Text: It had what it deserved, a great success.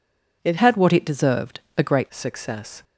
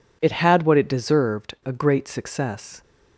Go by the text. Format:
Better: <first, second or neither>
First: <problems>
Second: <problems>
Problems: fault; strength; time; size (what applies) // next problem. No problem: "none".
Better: second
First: changes voice from "had" to "great"; from 0.5 to 2.0 s; 1.5 s long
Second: none